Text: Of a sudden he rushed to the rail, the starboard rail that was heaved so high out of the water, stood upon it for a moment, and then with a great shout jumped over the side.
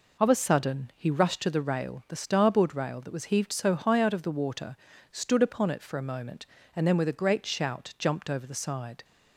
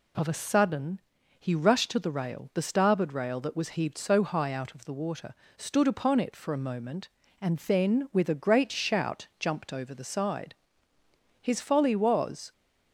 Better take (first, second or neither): first